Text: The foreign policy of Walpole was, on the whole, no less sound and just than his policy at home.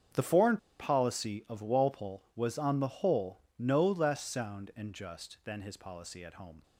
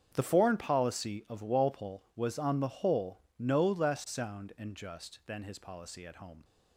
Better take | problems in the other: second | starts louder than the rest; strong; until 1.3 s; 7.5 dB; strong in the second // pauses between "foreign" and "policy"; slight; at 0.5 s; 0.21 s long

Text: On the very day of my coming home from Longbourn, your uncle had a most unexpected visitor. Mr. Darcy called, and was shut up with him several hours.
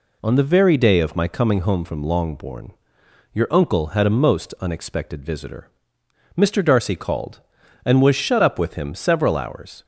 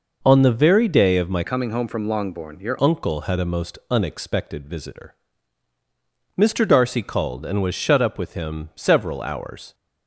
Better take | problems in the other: first | changes voice from "coming" to "your"; from 1.4 to 2.7 s; 1.3 s long

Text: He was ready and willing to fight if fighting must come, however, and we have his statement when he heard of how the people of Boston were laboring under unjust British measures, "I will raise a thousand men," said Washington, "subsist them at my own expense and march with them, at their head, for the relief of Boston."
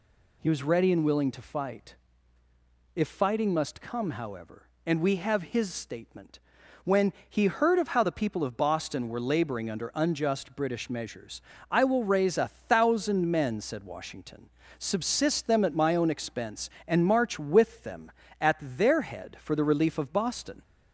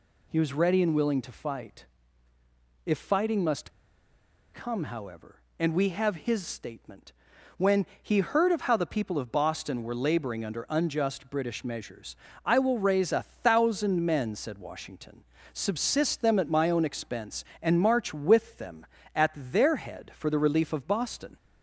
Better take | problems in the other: first | pauses between "fight" and "if"; at 1.8 s; 1.0 s long; also in the first // pauses between "must" and "come"; noticeable; at 3.7 s; 0.83 s long // pauses between "statement" and "when"; noticeable; at 7.1 s; 0.46 s long; noticeable in the first // pauses between "when" and "he"; slight; at 7.8 s; 0.16 s long; slight in the first

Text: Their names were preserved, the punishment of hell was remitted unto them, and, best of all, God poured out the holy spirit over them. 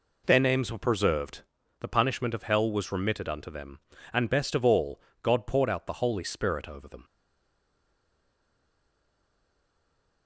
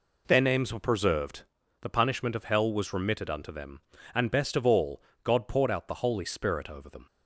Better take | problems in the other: second | stays silent after the last word; strong; from 7.0 s on; 3.2 s long

